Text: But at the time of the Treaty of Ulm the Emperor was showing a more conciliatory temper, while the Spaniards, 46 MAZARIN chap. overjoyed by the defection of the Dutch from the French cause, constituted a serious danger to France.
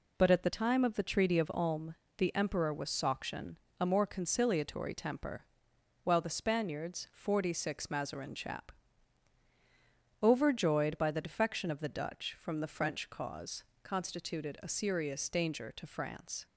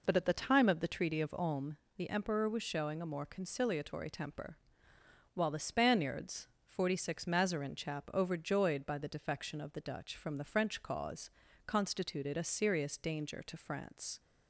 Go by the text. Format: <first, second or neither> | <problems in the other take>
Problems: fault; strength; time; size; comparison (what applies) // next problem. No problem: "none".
second | pauses between "Ulm" and "the"; slight; at 1.9 s; 0.22 s long; slight in the second // says "sauction" for "showing"; at 2.8 s